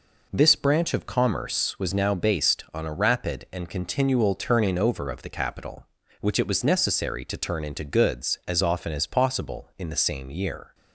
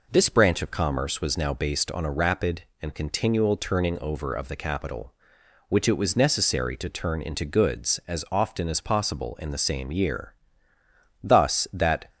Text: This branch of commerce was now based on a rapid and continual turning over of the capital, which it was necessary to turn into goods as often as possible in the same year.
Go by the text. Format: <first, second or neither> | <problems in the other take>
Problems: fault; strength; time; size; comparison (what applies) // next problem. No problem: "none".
first | goes on to say "Thus that"; noticeable; from 11.2 s on; 0.88 s long